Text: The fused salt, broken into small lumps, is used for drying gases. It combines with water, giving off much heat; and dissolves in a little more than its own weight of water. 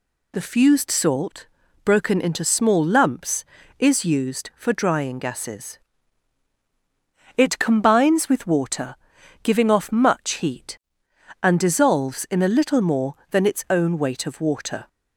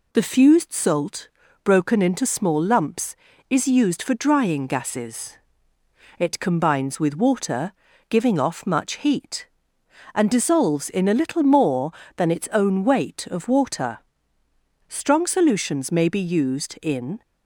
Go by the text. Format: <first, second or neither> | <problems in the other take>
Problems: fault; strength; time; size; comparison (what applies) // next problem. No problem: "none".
first | goes on to say "Strong solutions may be used in"; strong; from 14.8 s on; 2.3 s long